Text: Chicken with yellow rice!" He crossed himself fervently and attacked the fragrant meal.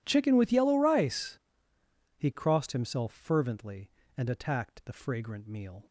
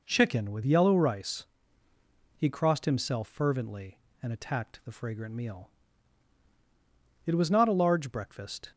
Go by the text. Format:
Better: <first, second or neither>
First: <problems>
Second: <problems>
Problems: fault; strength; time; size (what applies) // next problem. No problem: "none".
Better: first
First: none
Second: goes on to say "It was not a large breakfast"; from 7.2 s on; 1.4 s long